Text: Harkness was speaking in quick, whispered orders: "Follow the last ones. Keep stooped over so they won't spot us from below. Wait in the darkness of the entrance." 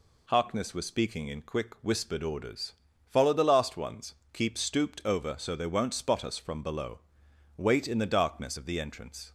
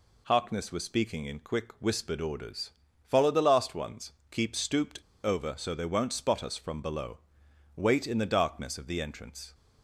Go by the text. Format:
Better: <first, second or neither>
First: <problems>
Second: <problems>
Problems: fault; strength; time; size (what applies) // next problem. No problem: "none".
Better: first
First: none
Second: pauses between "stooped" and "over"; slight; at 4.9 s; 0.27 s long